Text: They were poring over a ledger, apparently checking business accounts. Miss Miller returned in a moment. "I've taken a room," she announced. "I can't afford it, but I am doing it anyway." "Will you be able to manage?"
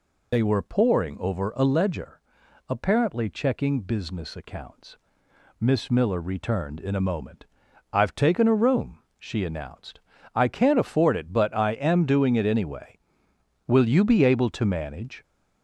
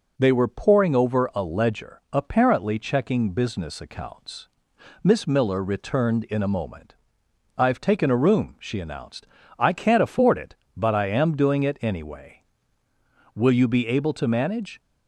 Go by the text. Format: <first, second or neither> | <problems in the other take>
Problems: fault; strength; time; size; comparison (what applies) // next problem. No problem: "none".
second | loses the start of "They"; at 0.3 s; 50 ms